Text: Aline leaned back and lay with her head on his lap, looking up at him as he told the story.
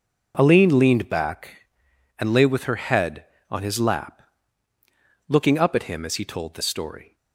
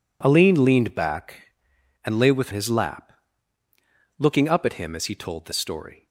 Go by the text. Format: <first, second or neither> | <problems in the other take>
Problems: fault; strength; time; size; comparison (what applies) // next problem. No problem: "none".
first | skips "her head on"; at 2.5 s